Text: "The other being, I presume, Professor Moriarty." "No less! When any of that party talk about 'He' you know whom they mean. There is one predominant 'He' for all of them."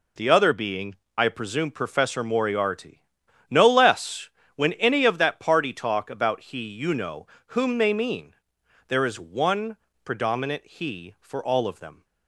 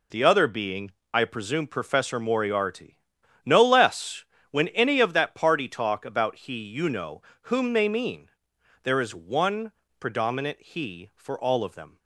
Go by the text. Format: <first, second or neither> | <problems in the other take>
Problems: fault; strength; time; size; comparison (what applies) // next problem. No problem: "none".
neither | pauses between "know" and "whom"; slight; the same in both // pauses between "one" and "predominant"; slight; the same in both